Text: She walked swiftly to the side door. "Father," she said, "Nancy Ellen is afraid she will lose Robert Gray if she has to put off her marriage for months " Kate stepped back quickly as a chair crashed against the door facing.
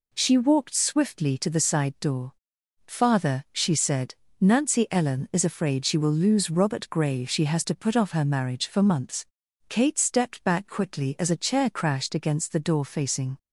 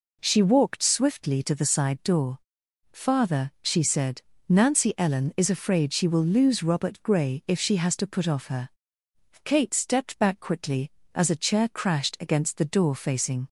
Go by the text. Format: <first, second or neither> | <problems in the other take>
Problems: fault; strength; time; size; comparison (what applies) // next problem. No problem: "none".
first | skips "marriage for months"; at 8.8 s